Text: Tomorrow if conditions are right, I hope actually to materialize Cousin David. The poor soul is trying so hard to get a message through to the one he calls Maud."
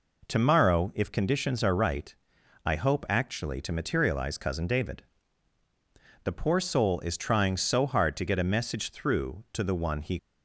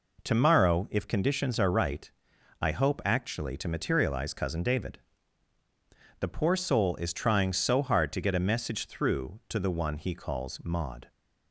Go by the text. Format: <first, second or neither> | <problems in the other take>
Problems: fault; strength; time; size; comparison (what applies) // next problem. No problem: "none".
second | stops before "calls Maud"; at 10.1 s